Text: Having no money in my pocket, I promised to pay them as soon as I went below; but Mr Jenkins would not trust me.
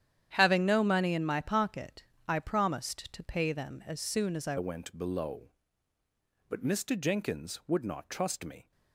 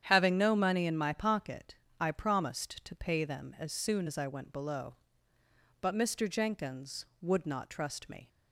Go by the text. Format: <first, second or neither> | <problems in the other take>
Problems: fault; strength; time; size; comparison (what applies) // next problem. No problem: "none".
second | starts louder than the rest; strong; until 1.3 s; 10 dB; strong in the second // changes voice at "went"; from 4.5 s on; 4.2 s long